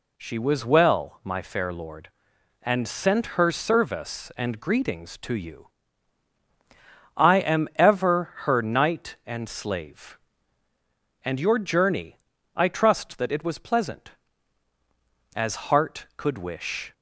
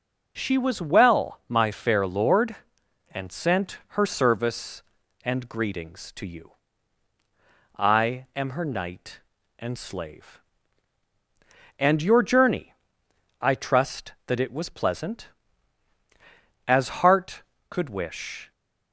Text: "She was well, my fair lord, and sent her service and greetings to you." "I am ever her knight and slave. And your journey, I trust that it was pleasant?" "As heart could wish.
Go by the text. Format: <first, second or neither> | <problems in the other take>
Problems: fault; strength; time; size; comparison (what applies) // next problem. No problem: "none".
first | pauses between "sent" and "her"; slight; at 3.7 s; 0.18 s long // skips "ever"; at 8.4 s